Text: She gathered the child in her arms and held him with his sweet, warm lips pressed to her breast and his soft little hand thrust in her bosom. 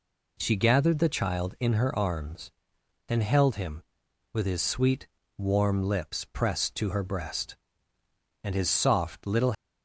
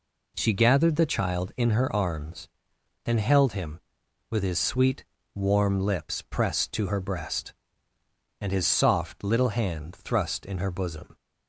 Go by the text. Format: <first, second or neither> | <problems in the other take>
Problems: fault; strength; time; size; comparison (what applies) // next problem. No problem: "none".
second | stops before "hand thrust in her bosom"; at 9.5 s